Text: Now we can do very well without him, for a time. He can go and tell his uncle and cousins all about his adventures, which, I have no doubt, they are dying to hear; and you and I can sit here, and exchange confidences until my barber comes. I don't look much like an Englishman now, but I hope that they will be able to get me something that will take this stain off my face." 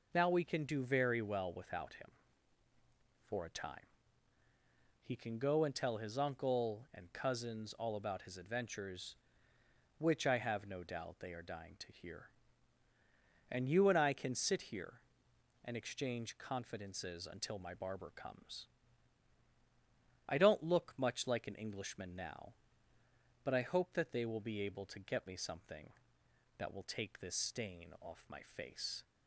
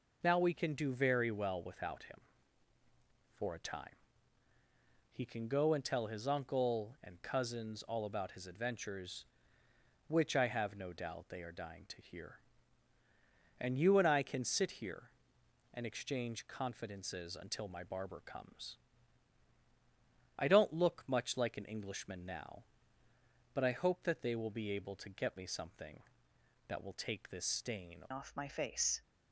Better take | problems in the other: first | changes voice at "off"; from 28.1 s on; 0.9 s long

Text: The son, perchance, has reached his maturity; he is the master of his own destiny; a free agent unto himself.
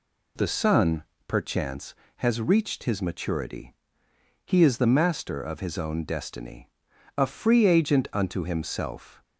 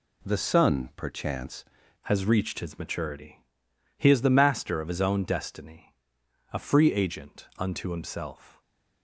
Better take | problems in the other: first | changes voice at "has"; from 2.0 s on; 6.6 s long // stays silent after the last word; slight; from 8.5 s on; 0.5 s long

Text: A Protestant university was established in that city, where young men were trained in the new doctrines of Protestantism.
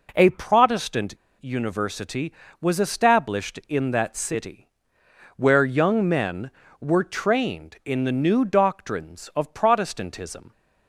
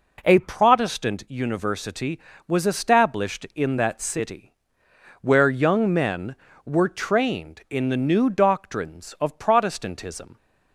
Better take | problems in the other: second | pauses between "Protestant" and "university"; slight; at 1.1 s; 0.27 s long

